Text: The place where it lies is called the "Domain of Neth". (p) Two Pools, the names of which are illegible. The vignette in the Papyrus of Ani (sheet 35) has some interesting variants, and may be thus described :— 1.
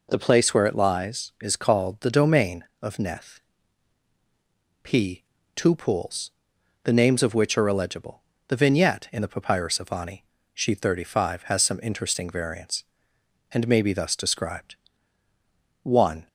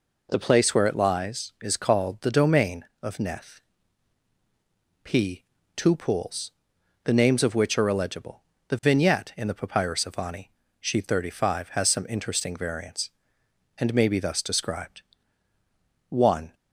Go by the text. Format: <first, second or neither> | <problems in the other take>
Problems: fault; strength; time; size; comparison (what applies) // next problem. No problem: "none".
neither | none